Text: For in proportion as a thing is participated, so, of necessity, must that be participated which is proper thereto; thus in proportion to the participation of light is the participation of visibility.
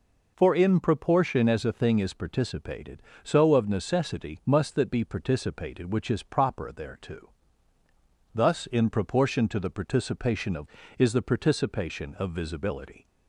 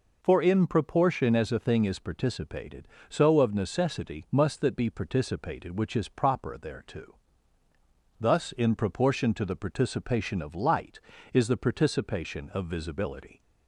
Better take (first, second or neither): second